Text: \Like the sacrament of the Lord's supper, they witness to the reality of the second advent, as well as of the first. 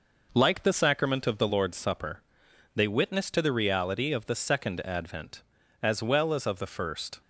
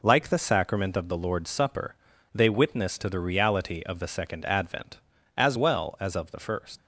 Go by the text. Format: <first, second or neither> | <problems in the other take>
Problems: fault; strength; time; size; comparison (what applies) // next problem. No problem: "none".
first | leaves "first" unfinished; at 6.7 s; 80 ms